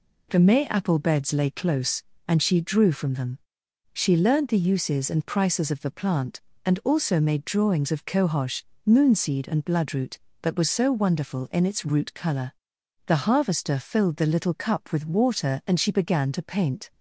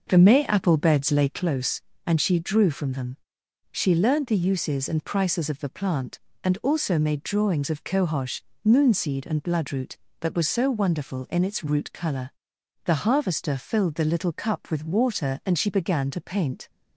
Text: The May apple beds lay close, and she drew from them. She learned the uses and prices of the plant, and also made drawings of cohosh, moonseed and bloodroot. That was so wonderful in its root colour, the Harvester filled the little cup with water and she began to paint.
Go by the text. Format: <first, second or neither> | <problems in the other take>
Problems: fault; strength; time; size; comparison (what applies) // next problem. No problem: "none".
first | starts louder than the rest; noticeable; until 1.5 s; 5.5 dB